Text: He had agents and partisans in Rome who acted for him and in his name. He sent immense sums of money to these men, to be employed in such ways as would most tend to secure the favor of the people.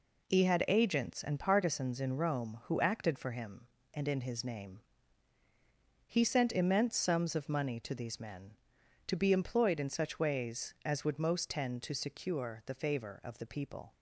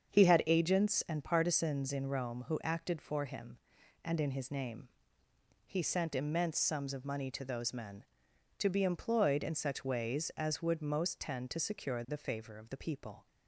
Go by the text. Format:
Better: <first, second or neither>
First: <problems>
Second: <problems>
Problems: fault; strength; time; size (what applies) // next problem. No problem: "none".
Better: first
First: none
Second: starts louder than the rest; strong; until 1.1 s; 7 dB // says "those" for "these"; at 7.4 s